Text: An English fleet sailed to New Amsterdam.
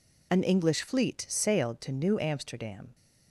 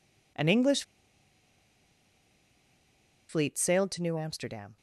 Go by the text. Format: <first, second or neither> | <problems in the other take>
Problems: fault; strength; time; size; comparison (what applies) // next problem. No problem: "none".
first | pauses between "English" and "fleet"; strong; at 0.8 s; 2.4 s long